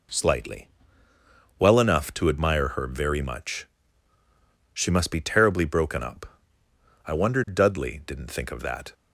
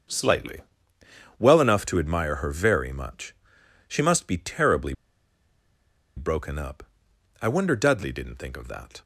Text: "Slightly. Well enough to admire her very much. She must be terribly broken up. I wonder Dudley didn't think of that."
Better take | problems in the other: first | starts louder than the rest; until 1.8 s; 6.5 dB // pauses between "terribly" and "broken"; at 4.9 s; 1.2 s long

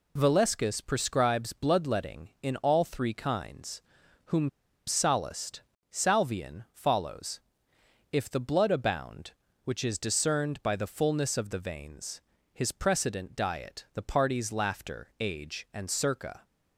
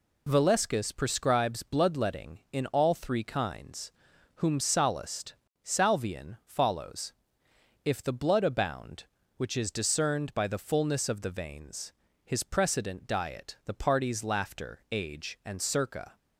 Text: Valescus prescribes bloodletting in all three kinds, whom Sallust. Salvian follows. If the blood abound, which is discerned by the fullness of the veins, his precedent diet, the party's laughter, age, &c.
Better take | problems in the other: second | pauses between "whom" and "Sallust"; at 4.4 s; 0.38 s long

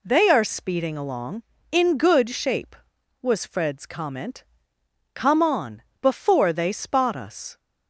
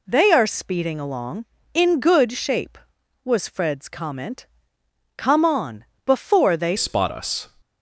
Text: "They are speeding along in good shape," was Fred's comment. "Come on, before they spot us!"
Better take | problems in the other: first | changes voice at "spot"; from 6.7 s on; 0.7 s long

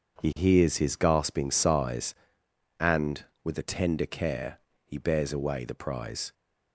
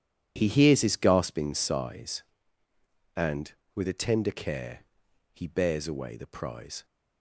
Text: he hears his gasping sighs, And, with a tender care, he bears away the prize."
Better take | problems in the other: neither | none

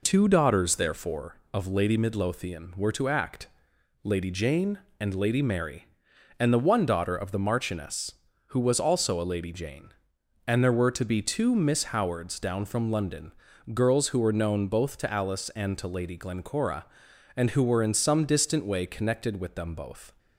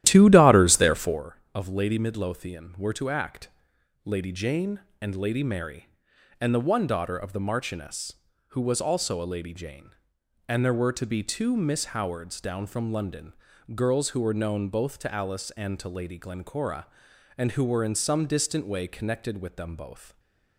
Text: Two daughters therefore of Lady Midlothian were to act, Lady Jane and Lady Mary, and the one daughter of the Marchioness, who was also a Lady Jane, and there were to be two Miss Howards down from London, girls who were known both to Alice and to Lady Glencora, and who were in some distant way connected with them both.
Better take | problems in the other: first | starts louder than the rest; strong; until 1.2 s; 13 dB // stays silent after the last word; slight; from 20.0 s on; 0.5 s long

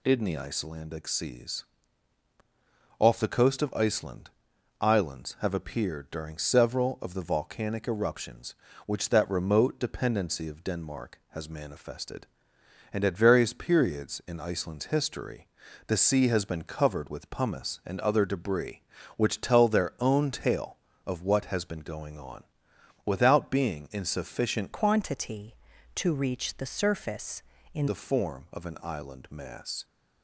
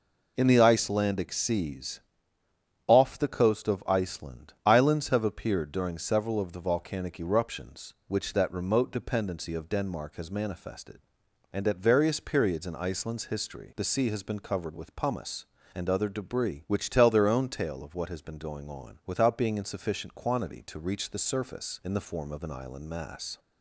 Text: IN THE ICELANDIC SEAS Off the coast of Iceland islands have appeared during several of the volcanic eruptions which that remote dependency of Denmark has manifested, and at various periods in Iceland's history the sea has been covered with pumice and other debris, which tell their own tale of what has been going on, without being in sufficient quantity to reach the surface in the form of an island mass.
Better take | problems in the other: second | pauses between "SEAS" and "Off"; strong; at 1.6 s; 1.3 s long; noticeable in the second // pauses between "Iceland" and "islands"; noticeable; at 4.3 s; 0.50 s long // pauses between "history" and "the"; at 15.4 s; 0.40 s long // changes voice from "quantity" to "in"; from 24.7 to 27.8 s; 3.1 s long

